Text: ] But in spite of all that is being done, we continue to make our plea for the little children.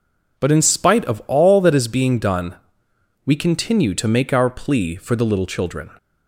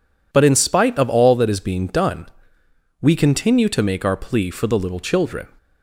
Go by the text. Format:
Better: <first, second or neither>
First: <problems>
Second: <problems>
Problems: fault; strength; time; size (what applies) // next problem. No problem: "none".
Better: neither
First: none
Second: none